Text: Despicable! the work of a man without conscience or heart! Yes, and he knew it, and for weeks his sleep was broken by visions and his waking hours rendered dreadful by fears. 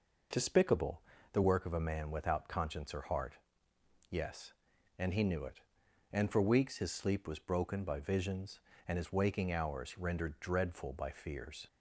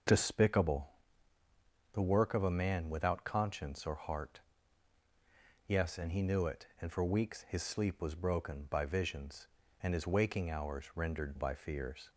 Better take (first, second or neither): first